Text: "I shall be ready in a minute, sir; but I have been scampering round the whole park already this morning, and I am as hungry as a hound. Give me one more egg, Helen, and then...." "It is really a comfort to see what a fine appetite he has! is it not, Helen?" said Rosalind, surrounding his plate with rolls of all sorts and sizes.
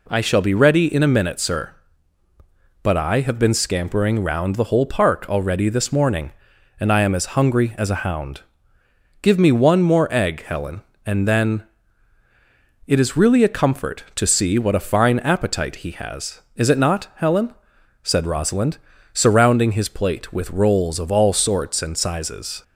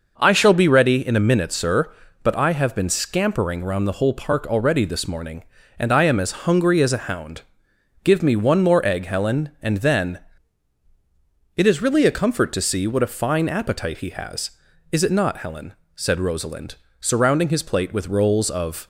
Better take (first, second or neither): first